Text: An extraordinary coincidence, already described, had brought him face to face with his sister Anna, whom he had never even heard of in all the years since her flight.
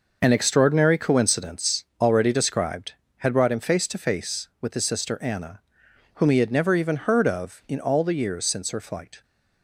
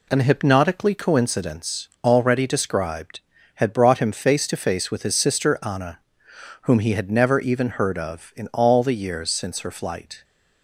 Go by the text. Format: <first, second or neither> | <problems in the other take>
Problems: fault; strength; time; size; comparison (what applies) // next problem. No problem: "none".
first | says "hypnotically" for "extraordinary"; at 0.2 s